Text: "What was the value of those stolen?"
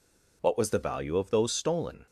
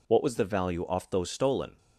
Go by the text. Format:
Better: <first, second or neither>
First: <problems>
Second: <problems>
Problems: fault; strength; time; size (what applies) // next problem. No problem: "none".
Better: first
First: none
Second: says "off" for "of"; at 0.8 s